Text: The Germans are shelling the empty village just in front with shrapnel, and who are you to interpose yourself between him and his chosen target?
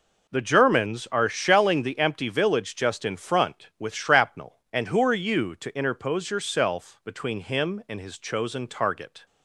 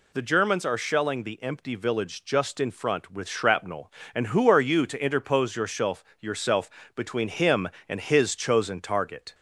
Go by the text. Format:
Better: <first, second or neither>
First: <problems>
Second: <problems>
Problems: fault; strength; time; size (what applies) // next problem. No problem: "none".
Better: first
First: none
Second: says "yourself" twice; at 6.2 s